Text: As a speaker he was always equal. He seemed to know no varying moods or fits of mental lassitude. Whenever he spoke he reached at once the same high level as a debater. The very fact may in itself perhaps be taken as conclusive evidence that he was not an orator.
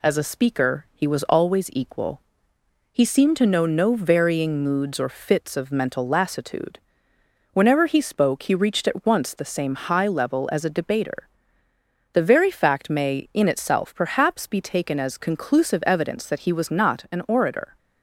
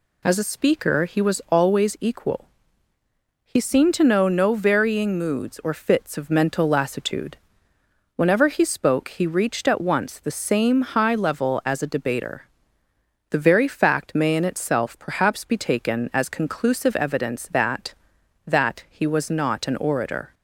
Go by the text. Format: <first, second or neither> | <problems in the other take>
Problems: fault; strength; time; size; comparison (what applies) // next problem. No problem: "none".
first | says "that" twice; at 18.4 s